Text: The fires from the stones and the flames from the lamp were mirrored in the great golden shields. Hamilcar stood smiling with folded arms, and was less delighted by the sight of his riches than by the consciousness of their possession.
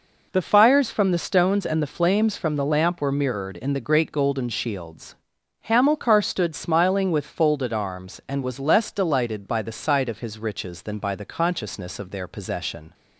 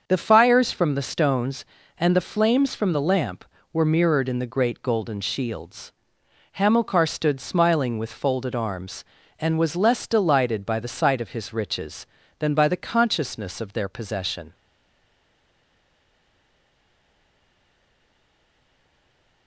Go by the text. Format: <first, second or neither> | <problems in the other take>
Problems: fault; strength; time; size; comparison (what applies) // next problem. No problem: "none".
first | starts louder than the rest; until 1.0 s; 6.5 dB // stays silent after the last word; strong; from 14.5 s on; 4.9 s long